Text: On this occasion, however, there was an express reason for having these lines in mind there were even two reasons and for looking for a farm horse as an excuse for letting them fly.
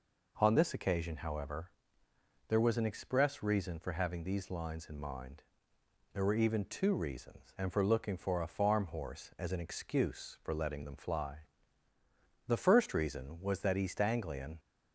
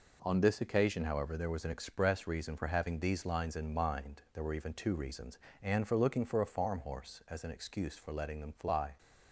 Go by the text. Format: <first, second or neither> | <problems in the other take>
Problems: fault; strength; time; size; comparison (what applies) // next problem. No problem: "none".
second | pauses between "mind" and "there"; noticeable; at 5.4 s; 0.70 s long // goes on to say "The first reason was that East Anglian"; strong; from 12.4 s on; 2.1 s long